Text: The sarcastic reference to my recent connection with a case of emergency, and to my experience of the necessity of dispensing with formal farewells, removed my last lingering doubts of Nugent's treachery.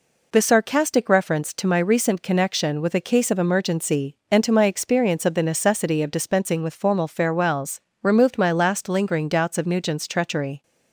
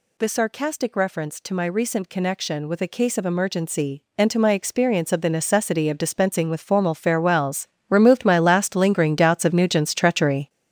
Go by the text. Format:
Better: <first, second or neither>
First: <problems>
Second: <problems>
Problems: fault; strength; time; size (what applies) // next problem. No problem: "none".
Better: first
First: none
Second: gets louder; strong; throughout; 8 dB